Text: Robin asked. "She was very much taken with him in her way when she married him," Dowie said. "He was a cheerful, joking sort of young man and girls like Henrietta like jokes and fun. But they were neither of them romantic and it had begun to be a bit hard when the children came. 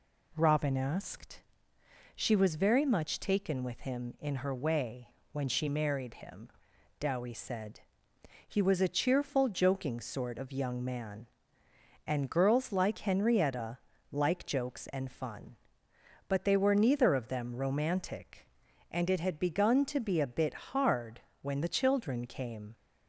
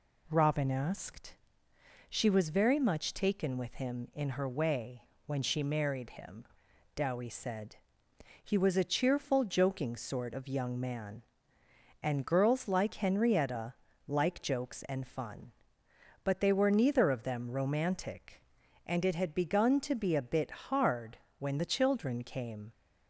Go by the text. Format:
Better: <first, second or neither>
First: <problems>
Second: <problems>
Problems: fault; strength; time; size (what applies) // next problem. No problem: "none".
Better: neither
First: pauses between "way" and "when"; slight; at 5.0 s; 0.24 s long // pauses between "Henrietta" and "like"; slight; at 13.7 s; 0.34 s long // pauses between "hard" and "when"; slight; at 21.2 s; 0.20 s long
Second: pauses between "way" and "when"; slight; at 5.0 s; 0.24 s long // pauses between "Henrietta" and "like"; slight; at 13.7 s; 0.34 s long // pauses between "hard" and "when"; slight; at 21.1 s; 0.20 s long